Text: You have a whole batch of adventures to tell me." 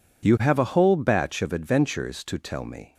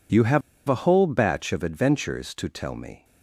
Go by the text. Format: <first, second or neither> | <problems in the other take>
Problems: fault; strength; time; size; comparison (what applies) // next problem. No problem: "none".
first | pauses between "have" and "a"; slight; at 0.4 s; 0.27 s long